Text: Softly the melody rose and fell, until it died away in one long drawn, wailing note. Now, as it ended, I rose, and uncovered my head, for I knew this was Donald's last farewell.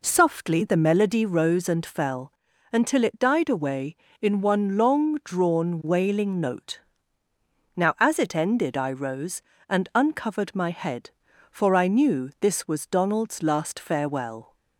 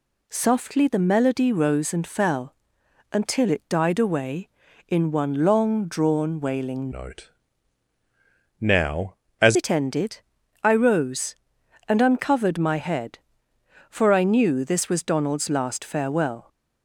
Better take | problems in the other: first | changes voice from "note" to "as"; from 6.9 to 9.5 s; 2.6 s long

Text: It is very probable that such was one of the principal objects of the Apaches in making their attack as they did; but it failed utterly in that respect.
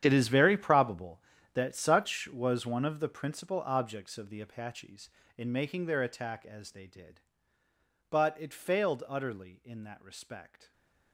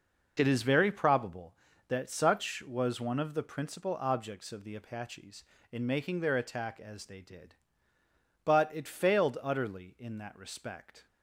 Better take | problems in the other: second | gets quieter; strong; throughout; 17 dB

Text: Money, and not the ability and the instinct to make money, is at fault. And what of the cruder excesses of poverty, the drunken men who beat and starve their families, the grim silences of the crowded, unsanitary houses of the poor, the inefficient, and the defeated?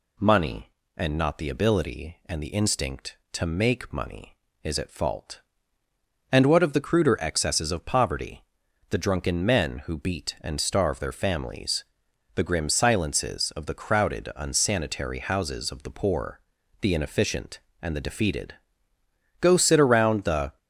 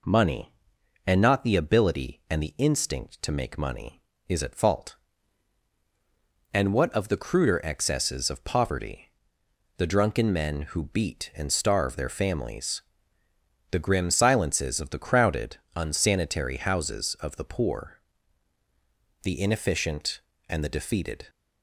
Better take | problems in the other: second | goes on to say "Go sit around the"; noticeable; from 19.3 s on; 1.1 s long

